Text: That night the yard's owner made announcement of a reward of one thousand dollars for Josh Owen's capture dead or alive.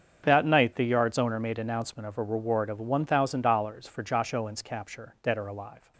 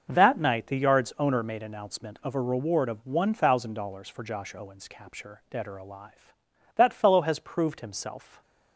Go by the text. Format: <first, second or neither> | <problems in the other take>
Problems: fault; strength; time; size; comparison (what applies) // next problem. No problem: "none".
first | starts louder than the rest; until 1.1 s; 6 dB; strong in the first // goes on to say "That fellow has proved himself"; from 6.7 s on; 1.6 s long